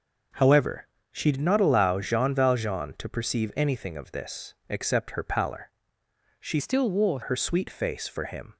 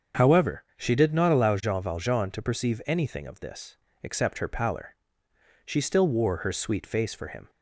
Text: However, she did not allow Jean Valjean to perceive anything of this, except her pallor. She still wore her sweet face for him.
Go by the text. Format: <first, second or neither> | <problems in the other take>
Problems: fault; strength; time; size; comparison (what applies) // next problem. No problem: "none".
second | starts louder than the rest; noticeable; until 1.5 s; 6 dB; also in the second // changes voice from "still" to "wore"; from 6.5 to 7.1 s; 0.6 s long